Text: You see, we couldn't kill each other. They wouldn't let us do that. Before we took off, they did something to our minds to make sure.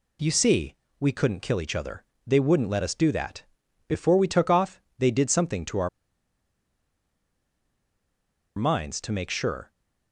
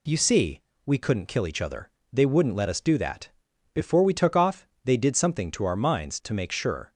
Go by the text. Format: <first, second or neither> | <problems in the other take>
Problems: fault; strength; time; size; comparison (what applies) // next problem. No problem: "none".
second | pauses between "our" and "minds"; strong; at 5.8 s; 2.6 s long